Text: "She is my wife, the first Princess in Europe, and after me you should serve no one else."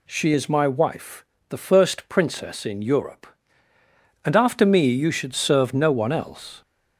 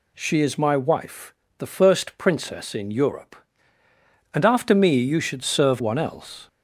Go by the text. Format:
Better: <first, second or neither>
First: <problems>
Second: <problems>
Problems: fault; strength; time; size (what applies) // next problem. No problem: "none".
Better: first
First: none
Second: skips "no"; at 5.8 s